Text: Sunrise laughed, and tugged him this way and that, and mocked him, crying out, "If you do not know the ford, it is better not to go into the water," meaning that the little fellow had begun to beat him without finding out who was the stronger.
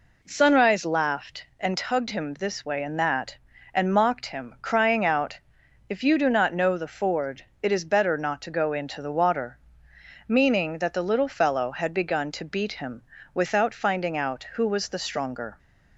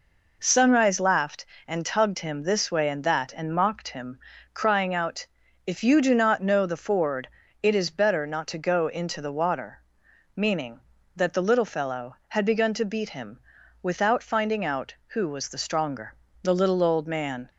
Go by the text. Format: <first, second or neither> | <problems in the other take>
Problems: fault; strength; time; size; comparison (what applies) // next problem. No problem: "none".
first | pauses between "him" and "without"; at 13.4 s; 0.42 s long; slight in the first // goes on to say "The little old man"; noticeable; from 16.4 s on; 1.0 s long